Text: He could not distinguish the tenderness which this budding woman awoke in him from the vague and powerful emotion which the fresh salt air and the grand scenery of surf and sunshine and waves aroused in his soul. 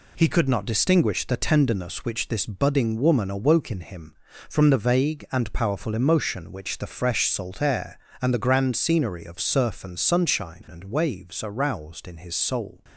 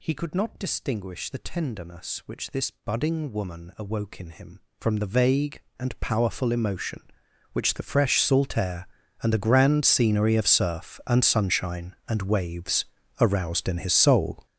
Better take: first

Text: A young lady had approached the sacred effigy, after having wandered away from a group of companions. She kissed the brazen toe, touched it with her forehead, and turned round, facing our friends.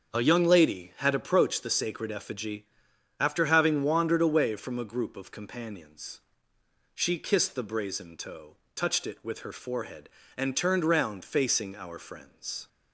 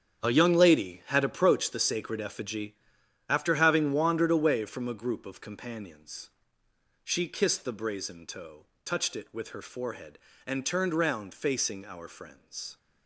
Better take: first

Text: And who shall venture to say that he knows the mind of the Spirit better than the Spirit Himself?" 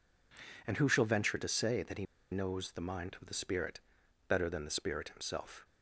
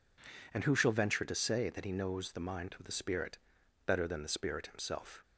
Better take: second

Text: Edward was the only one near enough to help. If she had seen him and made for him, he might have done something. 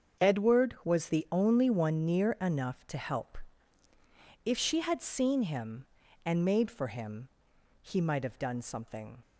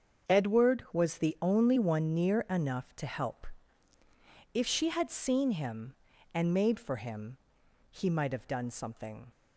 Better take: neither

